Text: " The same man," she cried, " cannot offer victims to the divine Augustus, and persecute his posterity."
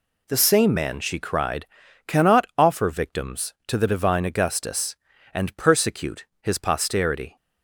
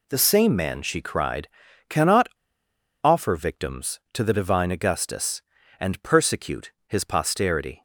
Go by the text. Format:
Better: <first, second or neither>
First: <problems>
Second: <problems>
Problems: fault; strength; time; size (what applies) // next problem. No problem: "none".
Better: first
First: pauses between "persecute" and "his"; slight; at 6.2 s; 0.16 s long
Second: pauses between "cannot" and "offer"; noticeable; at 2.2 s; 0.76 s long // pauses between "persecute" and "his"; slight; at 6.7 s; 0.16 s long